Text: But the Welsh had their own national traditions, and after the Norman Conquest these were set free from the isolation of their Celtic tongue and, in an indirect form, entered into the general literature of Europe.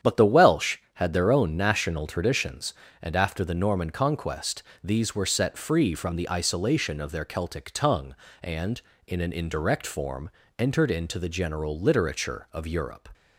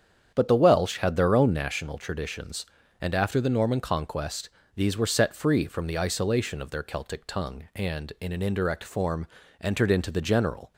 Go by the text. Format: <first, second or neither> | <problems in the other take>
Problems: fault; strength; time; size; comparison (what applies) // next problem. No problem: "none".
first | starts louder than the rest; strong; until 1.3 s; 8 dB; strong in the first // pauses between "Conquest" and "these"; slight; at 4.4 s; 0.26 s long; slight in the first // stops before "literature of Europe"; at 10.7 s